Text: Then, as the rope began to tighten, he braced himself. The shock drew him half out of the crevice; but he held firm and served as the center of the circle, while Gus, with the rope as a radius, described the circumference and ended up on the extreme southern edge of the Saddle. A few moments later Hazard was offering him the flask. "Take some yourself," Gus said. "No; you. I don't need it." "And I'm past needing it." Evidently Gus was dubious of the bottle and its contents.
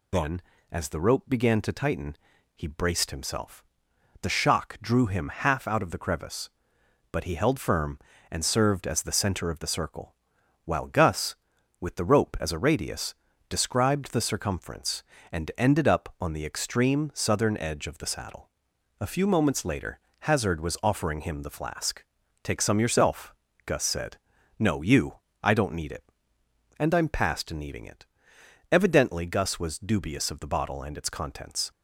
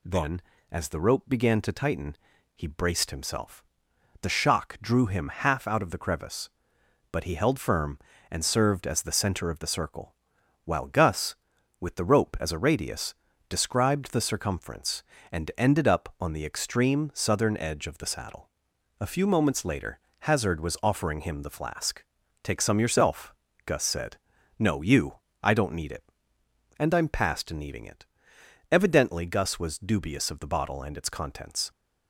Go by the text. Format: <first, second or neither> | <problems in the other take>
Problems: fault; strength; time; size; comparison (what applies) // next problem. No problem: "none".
second | loses the start of "Then"; at 0.1 s; 85 ms // pauses between "later" and "Hazard"; slight; at 20.0 s; 0.20 s long; slight in the second